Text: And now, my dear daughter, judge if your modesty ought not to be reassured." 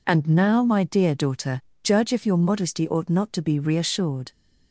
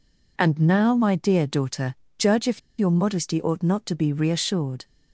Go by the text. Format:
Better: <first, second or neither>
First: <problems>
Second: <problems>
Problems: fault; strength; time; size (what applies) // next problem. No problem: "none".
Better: first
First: none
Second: pauses between "if" and "your"; slight; at 2.5 s; 0.18 s long